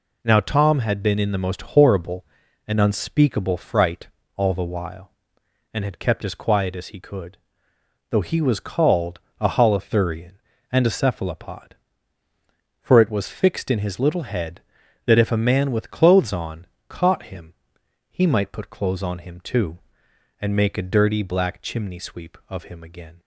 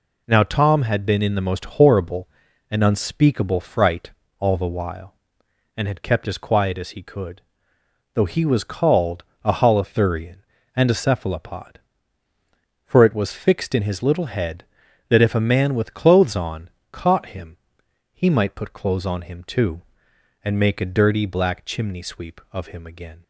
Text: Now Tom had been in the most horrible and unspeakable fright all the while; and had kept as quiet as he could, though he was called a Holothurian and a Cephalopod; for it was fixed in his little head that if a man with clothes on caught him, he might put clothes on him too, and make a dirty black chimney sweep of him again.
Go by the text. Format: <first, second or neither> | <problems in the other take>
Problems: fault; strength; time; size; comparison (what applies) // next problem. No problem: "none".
neither | pauses between "fright" and "all"; slight; the same in both // pauses between "called" and "a"; slight; the same in both // pauses between "on" and "caught"; slight; the same in both